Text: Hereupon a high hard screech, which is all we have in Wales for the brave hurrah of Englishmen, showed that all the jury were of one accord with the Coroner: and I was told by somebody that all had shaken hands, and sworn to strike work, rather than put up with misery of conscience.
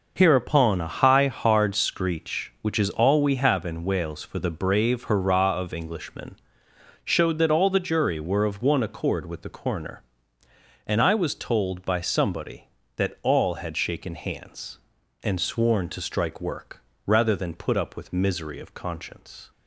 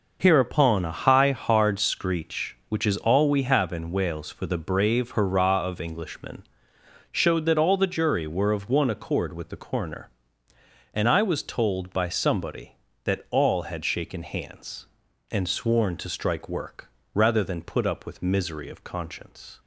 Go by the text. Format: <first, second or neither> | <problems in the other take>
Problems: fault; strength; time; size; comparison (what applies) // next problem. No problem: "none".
neither | none